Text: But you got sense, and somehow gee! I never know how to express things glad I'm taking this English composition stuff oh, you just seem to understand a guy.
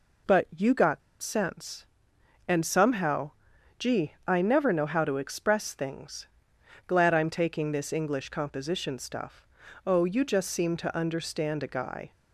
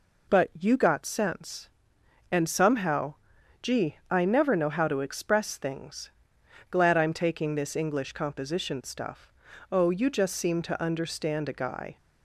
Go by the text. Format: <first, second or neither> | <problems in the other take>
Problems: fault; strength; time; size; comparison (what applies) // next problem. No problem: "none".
second | pauses between "got" and "sense"; slight; at 1.0 s; 0.22 s long // pauses between "somehow" and "gee"; noticeable; at 3.3 s; 0.48 s long; noticeable in the second // pauses between "things" and "glad"; noticeable; at 6.2 s; 0.60 s long; noticeable in the second // pauses between "stuff" and "oh"; at 9.4 s; 0.40 s long; also in the second